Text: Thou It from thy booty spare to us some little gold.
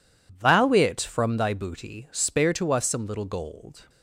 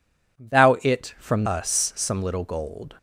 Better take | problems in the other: first | skips "thy booty spare to"; at 1.4 s

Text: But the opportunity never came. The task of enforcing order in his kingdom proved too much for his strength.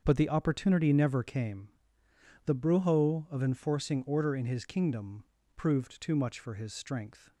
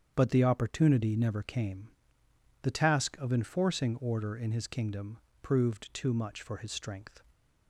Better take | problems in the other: second | starts louder than the rest; until 1.0 s; 6.5 dB; strong in the second // says "brujo" for "task"; at 2.5 s // pauses between "kingdom" and "proved"; slight; at 5.2 s; 0.32 s long; slight in the second

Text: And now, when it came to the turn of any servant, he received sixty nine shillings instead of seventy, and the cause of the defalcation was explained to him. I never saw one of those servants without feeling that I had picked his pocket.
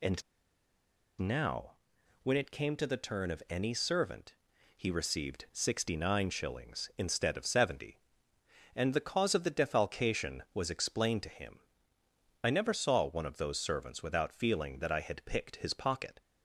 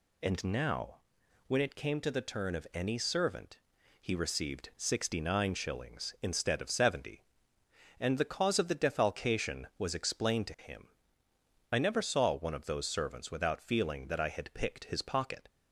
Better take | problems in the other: second | pauses between "And" and "now"; at 0.2 s; 0.98 s long

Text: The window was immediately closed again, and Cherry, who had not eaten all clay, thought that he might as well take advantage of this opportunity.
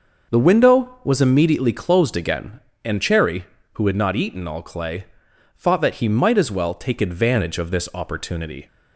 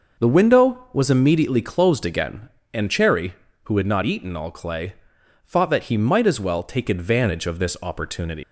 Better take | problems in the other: first | leaves "opportunity" unfinished; at 8.4 s; 120 ms

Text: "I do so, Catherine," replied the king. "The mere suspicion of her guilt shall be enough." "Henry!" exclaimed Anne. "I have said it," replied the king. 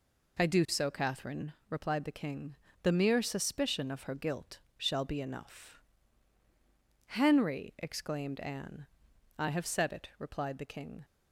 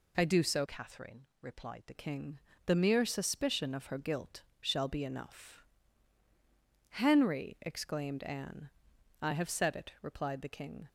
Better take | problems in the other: first | changes voice from "Catherine" to "the"; from 0.6 to 1.9 s; 1.3 s long // pauses between "guilt" and "shall"; slight; at 4.4 s; 0.20 s long; slight in the first

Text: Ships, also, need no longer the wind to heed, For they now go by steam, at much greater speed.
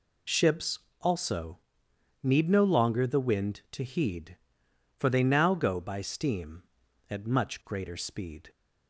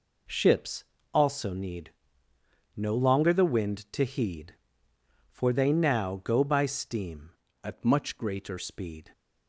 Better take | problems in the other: first | pauses between "need" and "no"; noticeable; at 1.9 s; 0.84 s long // changes voice from "at" to "greater"; from 7.6 to 8.5 s; 0.9 s long

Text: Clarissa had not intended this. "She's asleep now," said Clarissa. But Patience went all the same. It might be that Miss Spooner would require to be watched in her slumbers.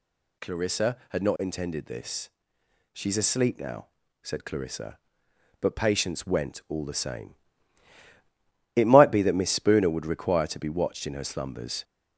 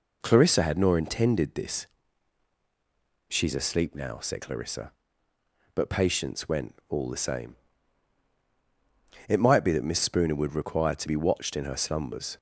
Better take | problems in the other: first | says "nor" for "not"; at 0.7 s

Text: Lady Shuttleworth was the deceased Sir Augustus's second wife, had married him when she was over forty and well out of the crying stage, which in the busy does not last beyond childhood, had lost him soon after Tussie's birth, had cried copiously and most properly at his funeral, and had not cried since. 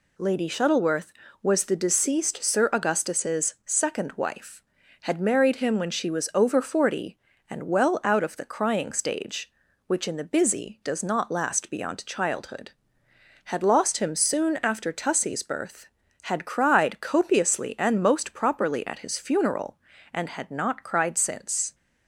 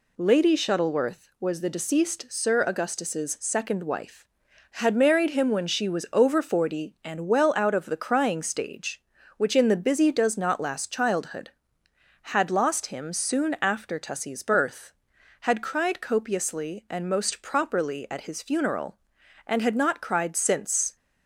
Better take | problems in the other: first | skips "beyond"; at 10.9 s

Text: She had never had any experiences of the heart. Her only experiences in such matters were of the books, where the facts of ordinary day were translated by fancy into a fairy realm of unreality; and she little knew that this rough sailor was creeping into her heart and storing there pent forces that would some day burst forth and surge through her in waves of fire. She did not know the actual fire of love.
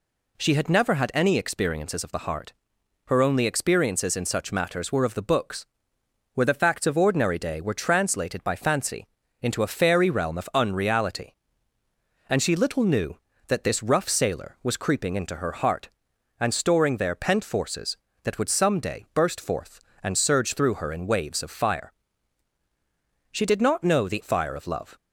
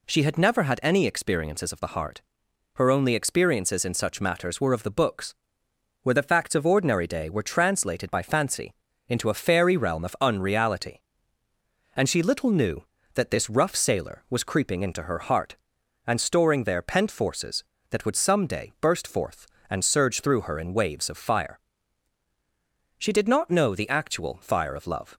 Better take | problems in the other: second | pauses between "fancy" and "into"; slight; at 9.0 s; 0.34 s long; slight in the second // skips "actual"; at 24.2 s

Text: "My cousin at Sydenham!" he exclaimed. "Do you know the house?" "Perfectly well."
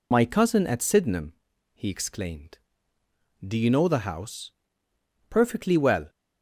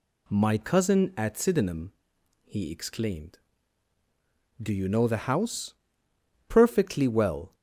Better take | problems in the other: second | loses the start of "My"; at 0.1 s; 60 ms

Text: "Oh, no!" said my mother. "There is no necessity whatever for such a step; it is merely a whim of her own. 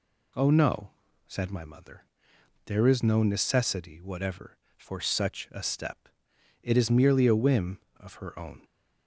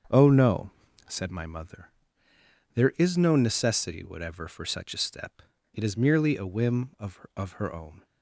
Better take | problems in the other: first | starts louder than the rest; strong; until 1.5 s; 7 dB // says "of" twice; at 7.3 s

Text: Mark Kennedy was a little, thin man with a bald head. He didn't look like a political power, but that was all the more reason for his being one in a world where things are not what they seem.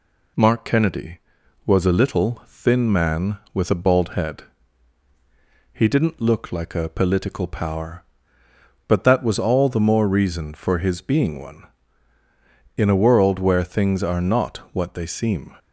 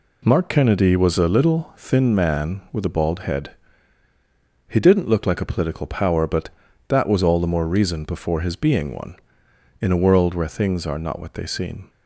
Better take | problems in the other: first | says "before" for "for"; at 8.0 s

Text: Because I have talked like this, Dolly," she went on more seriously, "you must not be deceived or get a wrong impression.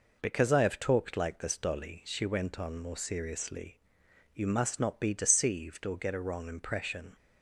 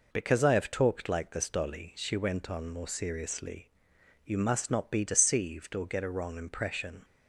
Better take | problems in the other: neither | none

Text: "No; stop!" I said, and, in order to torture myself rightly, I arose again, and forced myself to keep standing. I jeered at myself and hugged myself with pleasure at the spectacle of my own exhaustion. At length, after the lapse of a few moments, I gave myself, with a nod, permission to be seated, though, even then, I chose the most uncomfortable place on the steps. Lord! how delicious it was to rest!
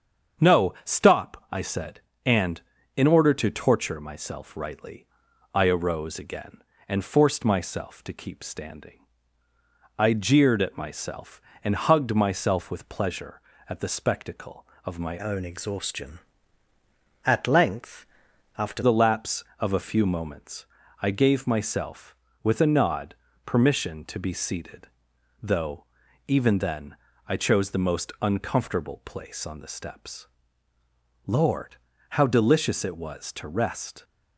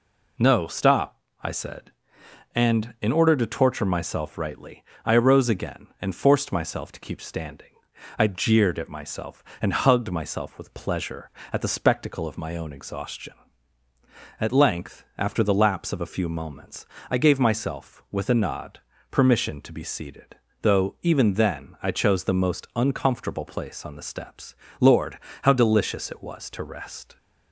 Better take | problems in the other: second | starts louder than the rest; strong; until 1.5 s; 7 dB // changes voice from "own" to "after"; from 15.1 to 18.8 s; 3.7 s long

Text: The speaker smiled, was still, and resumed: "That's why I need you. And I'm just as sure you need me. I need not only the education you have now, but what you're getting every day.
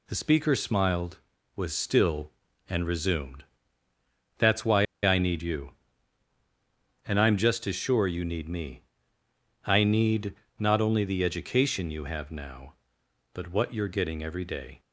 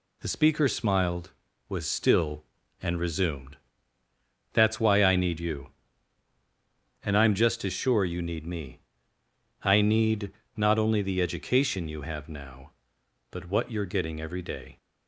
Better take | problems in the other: second | pauses between "why" and "I"; slight; at 4.8 s; 0.20 s long // pauses between "need" and "not"; slight; at 10.3 s; 0.24 s long; slight in the second

